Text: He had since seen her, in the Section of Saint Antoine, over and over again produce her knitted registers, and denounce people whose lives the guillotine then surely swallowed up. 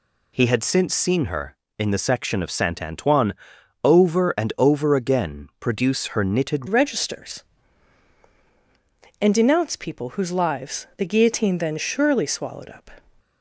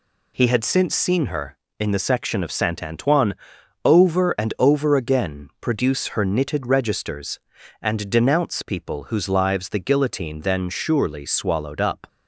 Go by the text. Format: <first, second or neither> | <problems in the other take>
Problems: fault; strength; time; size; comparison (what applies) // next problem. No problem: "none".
second | changes voice at "registers"; from 6.6 s on; 6.3 s long